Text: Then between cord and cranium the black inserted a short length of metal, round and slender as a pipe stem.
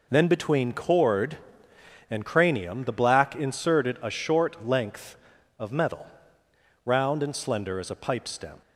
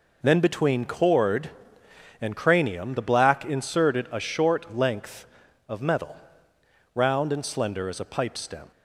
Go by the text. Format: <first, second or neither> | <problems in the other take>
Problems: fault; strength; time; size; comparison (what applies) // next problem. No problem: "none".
neither | none